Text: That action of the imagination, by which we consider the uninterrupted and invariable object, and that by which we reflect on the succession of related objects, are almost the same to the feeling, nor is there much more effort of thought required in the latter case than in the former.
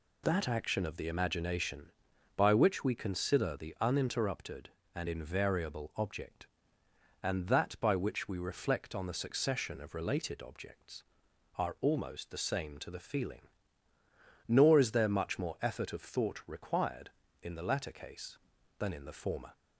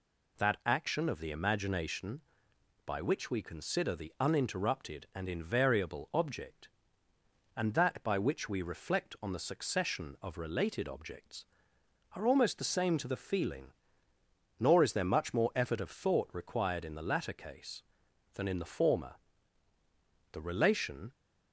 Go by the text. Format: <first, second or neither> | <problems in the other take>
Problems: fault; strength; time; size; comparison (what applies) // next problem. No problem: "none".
first | goes on to say "The relation"; noticeable; from 20.3 s on; 0.80 s long